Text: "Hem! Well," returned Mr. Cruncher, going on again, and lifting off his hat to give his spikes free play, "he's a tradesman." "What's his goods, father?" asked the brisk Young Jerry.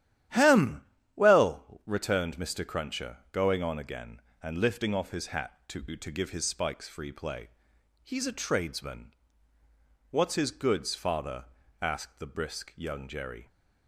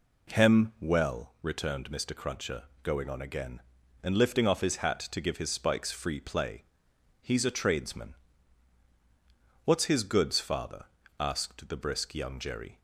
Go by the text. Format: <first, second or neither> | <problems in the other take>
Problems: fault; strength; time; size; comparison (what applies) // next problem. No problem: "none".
second | starts louder than the rest; strong; until 1.6 s; 11.5 dB // says "to" twice; at 5.9 s